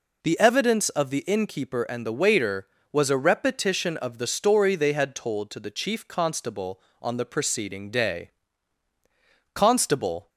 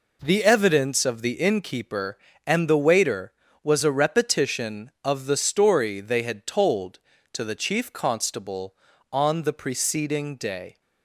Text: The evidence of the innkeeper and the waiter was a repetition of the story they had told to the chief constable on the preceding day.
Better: second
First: goes on to say "Constable"; noticeable; from 9.5 s on; 0.76 s long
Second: none

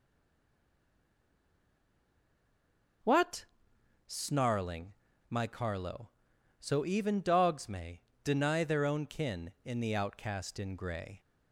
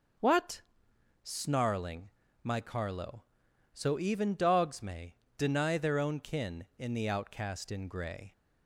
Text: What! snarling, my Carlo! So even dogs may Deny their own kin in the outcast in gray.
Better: second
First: stays silent before the first word; strong; until 3.0 s; 3.0 s long // starts louder than the rest; until 4.6 s; 6.5 dB // pauses between "may" and "Deny"; slight; at 7.9 s; 0.24 s long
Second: starts louder than the rest; until 1.8 s; 6.5 dB // pauses between "may" and "Deny"; slight; at 5.1 s; 0.24 s long

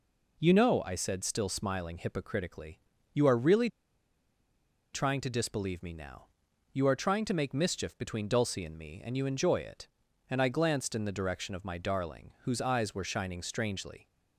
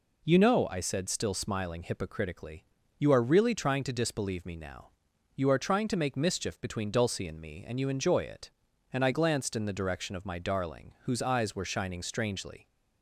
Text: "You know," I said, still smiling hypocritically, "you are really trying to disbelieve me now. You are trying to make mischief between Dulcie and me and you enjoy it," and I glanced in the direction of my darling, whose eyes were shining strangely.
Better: second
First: pauses between "really" and "trying"; strong; at 3.6 s; 1.2 s long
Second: none

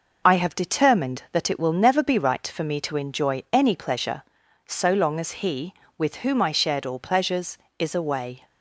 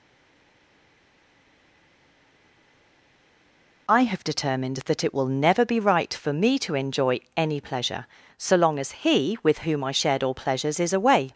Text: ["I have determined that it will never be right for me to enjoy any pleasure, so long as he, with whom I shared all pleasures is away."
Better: first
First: none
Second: stays silent before the first word; strong; until 3.8 s; 3.8 s long

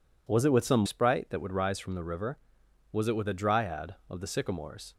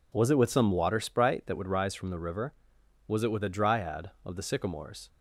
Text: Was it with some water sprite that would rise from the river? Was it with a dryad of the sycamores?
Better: second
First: skips "water"; at 0.8 s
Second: none

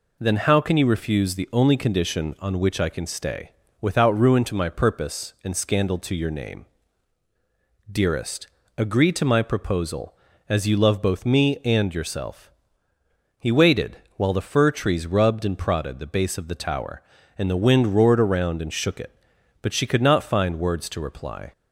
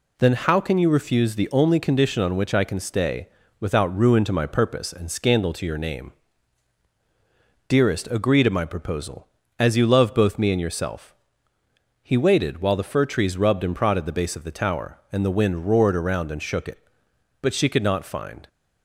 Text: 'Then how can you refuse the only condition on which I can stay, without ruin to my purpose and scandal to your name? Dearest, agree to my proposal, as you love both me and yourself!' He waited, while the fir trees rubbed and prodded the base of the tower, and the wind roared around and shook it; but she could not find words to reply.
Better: first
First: none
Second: stops before "words to reply"; at 18.4 s

